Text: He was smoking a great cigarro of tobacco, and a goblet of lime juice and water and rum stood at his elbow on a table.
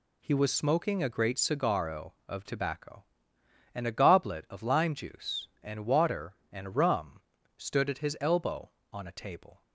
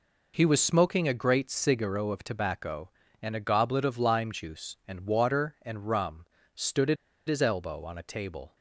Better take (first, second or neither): first